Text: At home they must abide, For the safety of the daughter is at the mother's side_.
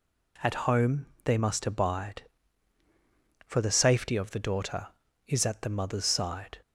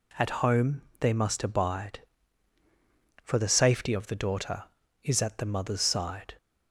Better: neither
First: pauses between "home" and "they"; slight; at 1.0 s; 0.18 s long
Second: pauses between "home" and "they"; slight; at 0.8 s; 0.18 s long

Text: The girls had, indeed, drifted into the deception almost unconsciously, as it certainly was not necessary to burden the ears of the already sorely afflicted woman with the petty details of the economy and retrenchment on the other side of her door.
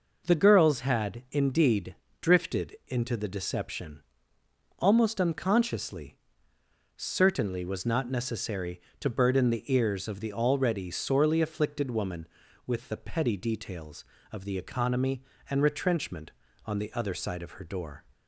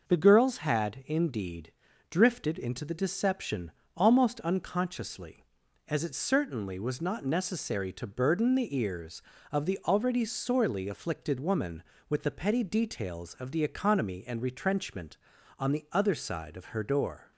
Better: second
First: pauses between "deception" and "almost"; noticeable; at 4.0 s; 0.76 s long // skips "as it"; at 6.5 s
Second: pauses between "deception" and "almost"; slight; at 3.7 s; 0.24 s long

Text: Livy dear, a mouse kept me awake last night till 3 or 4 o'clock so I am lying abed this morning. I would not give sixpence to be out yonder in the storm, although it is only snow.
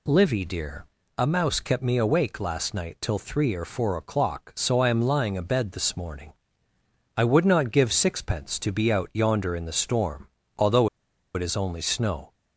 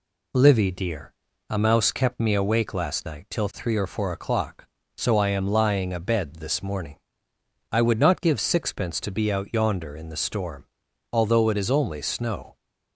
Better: second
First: pauses between "although" and "it"; noticeable; at 10.8 s; 0.47 s long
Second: none

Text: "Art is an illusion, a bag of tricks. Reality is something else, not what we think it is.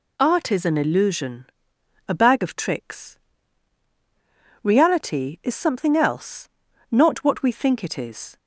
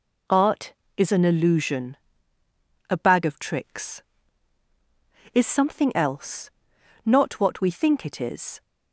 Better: first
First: none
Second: skips "Reality"; at 4.6 s

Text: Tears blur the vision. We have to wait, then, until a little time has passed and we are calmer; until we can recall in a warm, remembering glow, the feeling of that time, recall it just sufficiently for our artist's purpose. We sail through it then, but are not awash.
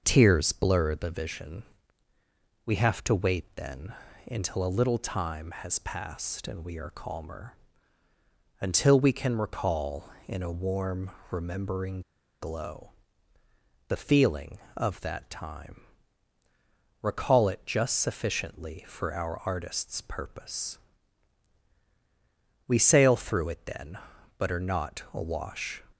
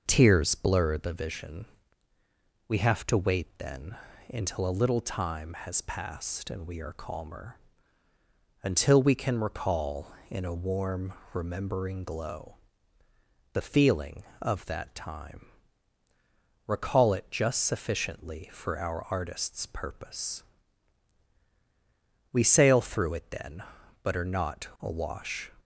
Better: second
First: pauses between "remembering" and "glow"; at 12.0 s; 0.38 s long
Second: none

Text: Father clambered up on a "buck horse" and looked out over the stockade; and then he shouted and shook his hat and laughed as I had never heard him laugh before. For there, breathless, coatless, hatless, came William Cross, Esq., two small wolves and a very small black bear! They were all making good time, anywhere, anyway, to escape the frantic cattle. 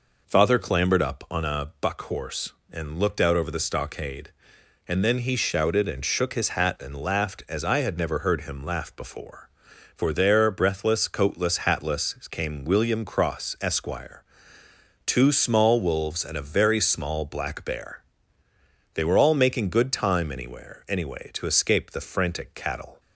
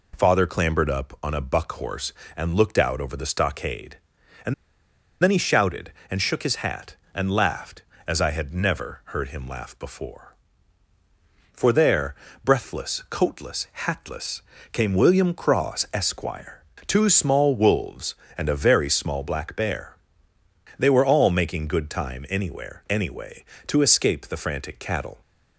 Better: first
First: none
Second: pauses between "and" and "then"; noticeable; at 4.5 s; 0.69 s long

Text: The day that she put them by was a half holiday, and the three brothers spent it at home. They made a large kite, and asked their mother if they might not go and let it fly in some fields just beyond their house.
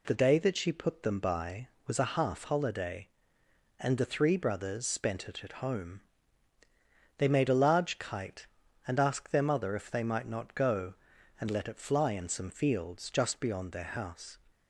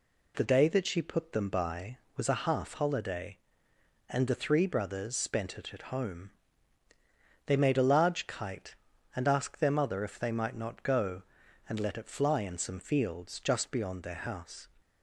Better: neither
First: none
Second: none

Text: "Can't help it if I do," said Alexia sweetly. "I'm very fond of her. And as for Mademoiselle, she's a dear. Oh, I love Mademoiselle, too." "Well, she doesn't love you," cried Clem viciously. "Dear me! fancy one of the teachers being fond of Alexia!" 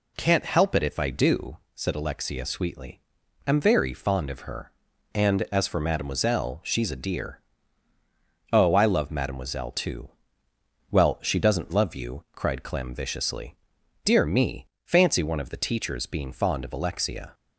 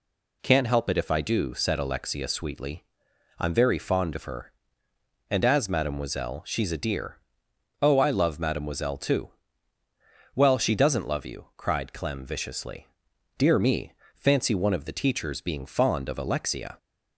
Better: first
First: none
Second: skips "for"; at 5.6 s

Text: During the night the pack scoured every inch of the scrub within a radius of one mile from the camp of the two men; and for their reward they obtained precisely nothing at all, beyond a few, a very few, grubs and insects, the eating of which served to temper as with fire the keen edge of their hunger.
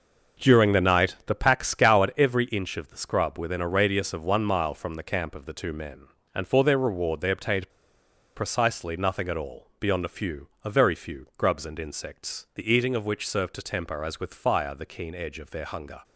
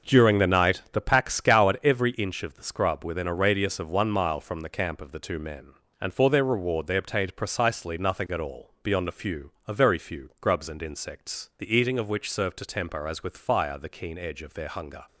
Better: second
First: starts louder than the rest; until 1.5 s; 6.5 dB // pauses between "obtained" and "precisely"; noticeable; at 7.7 s; 0.65 s long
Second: starts louder than the rest; until 1.1 s; 6.5 dB

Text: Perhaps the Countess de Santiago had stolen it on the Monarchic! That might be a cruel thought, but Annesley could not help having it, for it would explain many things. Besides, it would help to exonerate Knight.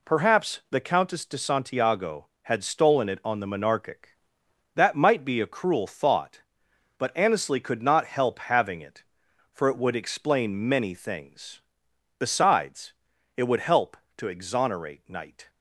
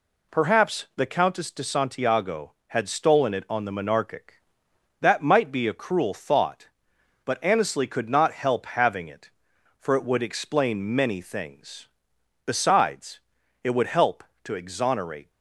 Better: first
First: none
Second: stops before "Knight"; at 15.3 s

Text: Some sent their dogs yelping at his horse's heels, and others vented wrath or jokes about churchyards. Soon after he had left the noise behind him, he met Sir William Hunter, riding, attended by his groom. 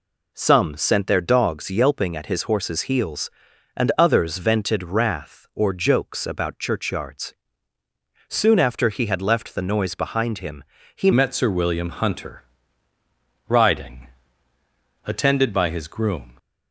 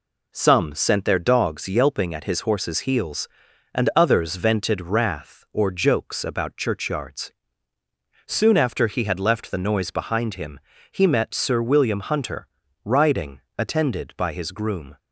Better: second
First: changes voice at "met"; from 11.1 s on; 5.2 s long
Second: none

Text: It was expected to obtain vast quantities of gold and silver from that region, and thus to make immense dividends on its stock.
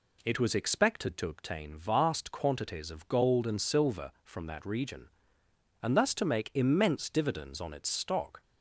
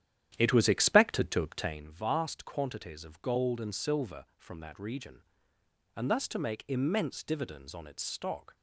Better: first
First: none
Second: starts louder than the rest; strong; until 1.9 s; 11 dB

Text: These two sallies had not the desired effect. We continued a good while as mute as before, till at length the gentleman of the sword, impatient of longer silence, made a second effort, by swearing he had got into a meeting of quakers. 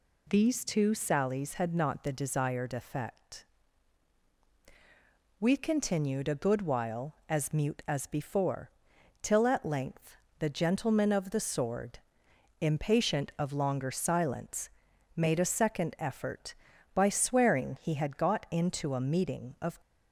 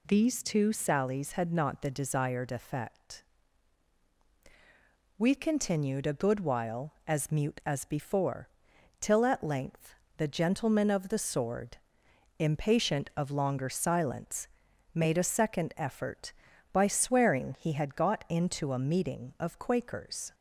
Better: second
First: pauses between "length" and "the"; slight; at 10.1 s; 0.22 s long // stops before "quakers"; at 19.8 s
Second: pauses between "length" and "the"; slight; at 9.9 s; 0.22 s long

